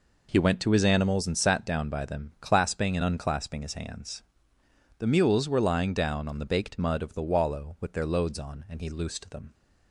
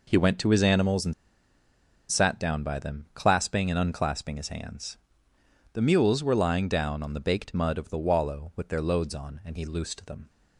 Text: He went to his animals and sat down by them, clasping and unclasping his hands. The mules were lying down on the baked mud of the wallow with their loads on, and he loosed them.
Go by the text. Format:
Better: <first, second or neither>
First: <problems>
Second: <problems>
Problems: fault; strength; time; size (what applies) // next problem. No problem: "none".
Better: first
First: none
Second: pauses between "and" and "sat"; noticeable; at 1.1 s; 0.95 s long